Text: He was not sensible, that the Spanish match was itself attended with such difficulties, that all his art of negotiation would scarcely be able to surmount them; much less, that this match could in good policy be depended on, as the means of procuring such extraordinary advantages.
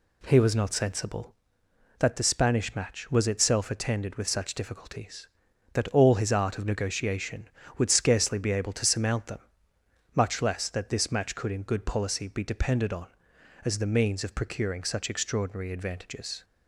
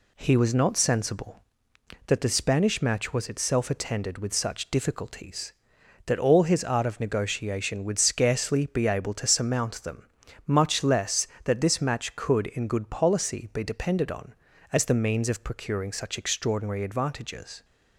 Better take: neither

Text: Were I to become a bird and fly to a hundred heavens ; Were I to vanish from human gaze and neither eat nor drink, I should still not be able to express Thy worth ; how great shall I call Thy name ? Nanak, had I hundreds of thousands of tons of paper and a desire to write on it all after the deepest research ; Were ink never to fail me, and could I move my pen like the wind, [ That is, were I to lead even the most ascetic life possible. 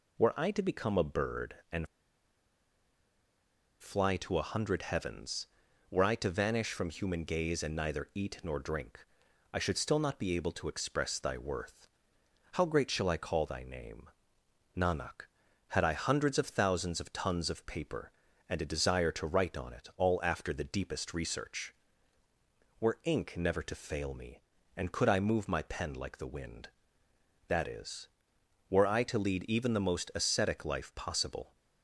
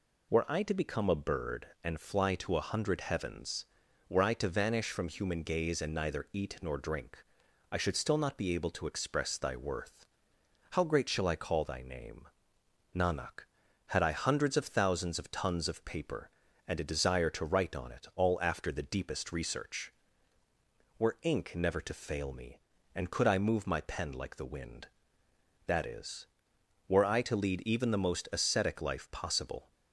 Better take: second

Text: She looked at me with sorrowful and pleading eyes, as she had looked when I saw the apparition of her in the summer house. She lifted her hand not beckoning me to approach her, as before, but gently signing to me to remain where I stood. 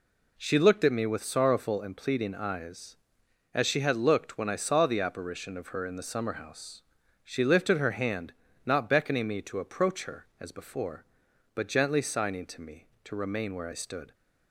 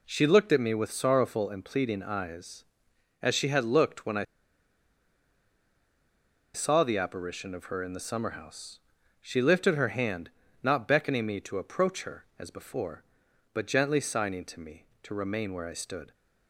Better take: first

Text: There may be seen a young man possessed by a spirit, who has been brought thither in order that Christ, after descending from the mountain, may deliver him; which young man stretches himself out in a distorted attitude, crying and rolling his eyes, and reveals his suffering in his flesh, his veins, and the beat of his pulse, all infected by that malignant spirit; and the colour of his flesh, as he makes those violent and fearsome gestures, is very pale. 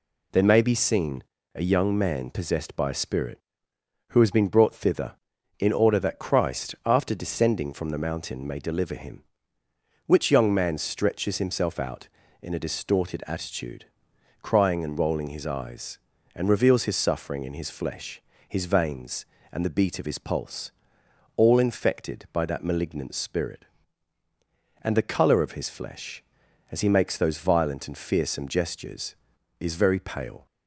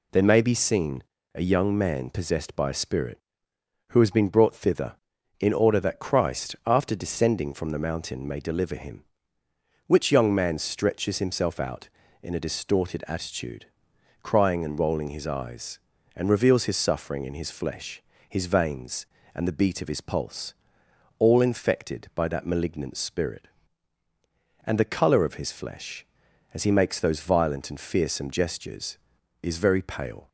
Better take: neither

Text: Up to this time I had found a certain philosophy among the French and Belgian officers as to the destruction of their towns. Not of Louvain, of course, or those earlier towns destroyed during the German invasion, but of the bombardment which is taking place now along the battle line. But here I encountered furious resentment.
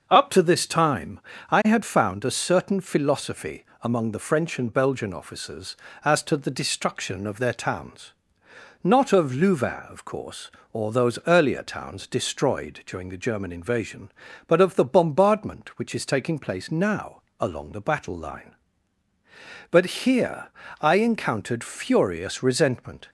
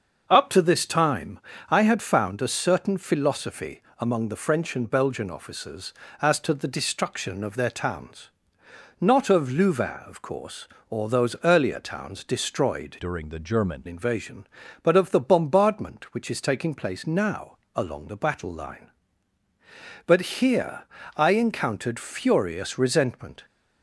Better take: first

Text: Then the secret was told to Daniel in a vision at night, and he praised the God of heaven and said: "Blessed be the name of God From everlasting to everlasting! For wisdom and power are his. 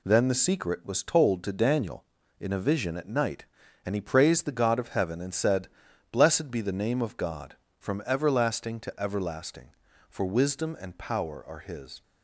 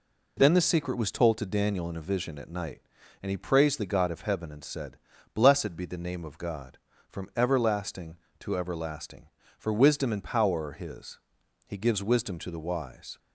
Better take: first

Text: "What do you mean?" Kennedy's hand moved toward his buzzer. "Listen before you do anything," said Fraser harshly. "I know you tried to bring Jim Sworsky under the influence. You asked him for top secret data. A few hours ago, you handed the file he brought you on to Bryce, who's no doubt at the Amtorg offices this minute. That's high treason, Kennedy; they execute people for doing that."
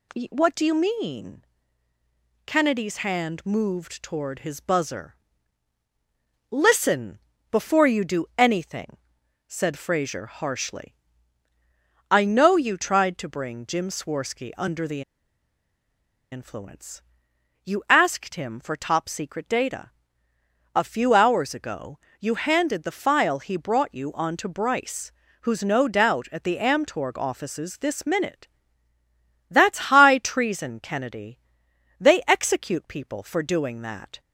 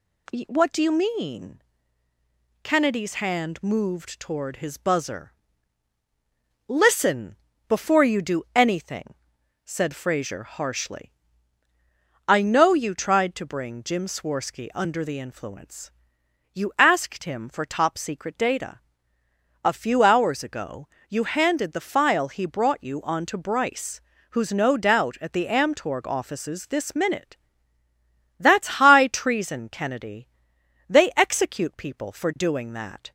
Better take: second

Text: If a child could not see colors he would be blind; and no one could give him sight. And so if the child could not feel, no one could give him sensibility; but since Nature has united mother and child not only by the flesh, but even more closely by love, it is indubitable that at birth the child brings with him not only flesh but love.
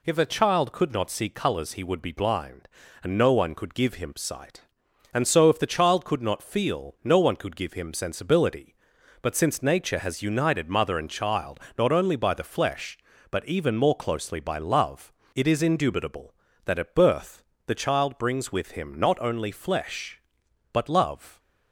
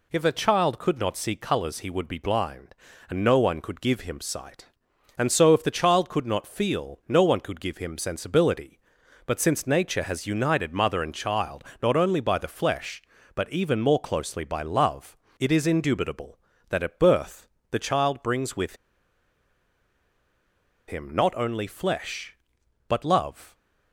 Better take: first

